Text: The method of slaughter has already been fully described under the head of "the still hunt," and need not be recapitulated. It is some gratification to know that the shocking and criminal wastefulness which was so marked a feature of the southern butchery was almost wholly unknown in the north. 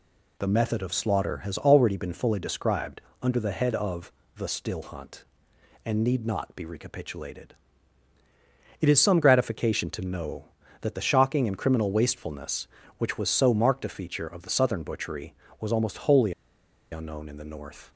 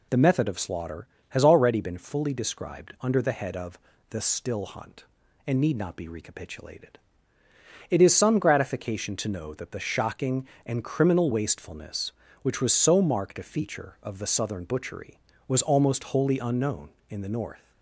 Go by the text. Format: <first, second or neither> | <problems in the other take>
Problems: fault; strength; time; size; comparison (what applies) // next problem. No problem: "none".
second | pauses between "described" and "under"; slight; at 3.0 s; 0.20 s long // pauses between "of" and "the"; slight; at 4.1 s; 0.26 s long; slight in the second // pauses between "wholly" and "unknown"; noticeable; at 16.3 s; 0.59 s long